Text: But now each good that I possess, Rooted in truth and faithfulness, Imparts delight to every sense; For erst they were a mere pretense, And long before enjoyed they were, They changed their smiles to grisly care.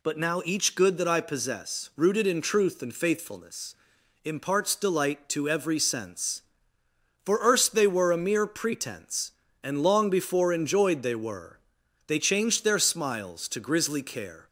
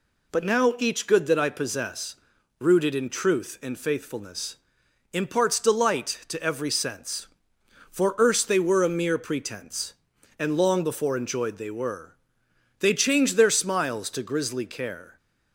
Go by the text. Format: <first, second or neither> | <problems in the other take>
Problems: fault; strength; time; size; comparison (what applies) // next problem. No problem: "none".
neither | none